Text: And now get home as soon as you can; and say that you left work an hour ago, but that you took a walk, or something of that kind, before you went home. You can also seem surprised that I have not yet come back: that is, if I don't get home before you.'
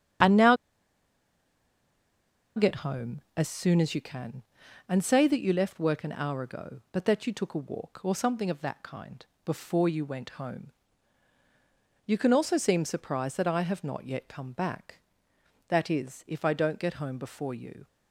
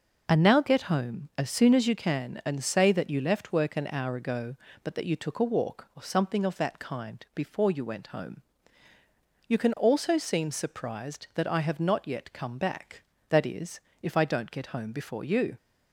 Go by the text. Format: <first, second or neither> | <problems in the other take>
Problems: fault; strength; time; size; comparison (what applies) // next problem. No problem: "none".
second | starts louder than the rest; strong; until 3.3 s; 8.5 dB // pauses between "now" and "get"; strong; at 0.5 s; 2.0 s long